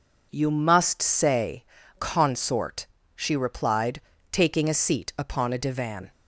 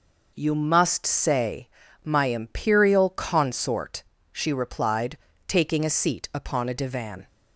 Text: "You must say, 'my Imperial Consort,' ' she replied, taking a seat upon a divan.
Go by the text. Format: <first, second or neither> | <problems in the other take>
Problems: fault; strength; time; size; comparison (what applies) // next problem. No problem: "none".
second | skips "my Imperial"; at 1.8 s